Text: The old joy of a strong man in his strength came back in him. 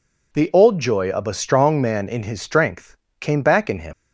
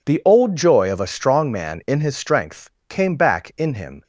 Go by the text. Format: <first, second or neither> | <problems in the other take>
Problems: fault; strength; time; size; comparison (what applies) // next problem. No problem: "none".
second | pauses between "strength" and "came"; slight; at 2.9 s; 0.24 s long; slight in the second // leaves "him" unfinished; at 3.9 s; 75 ms